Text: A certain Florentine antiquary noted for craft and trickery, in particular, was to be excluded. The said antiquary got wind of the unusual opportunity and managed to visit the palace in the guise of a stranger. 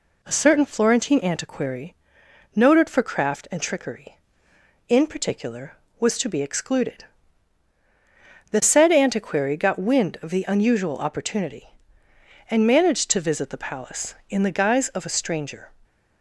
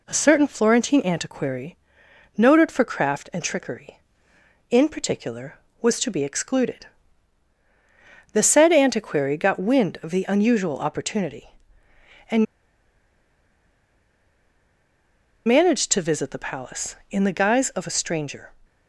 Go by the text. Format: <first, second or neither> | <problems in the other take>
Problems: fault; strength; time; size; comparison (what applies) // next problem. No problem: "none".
first | pauses between "antiquary" and "noted"; noticeable; at 1.7 s; 0.58 s long; noticeable in the first // pauses between "and" and "managed"; strong; at 12.4 s; 3.0 s long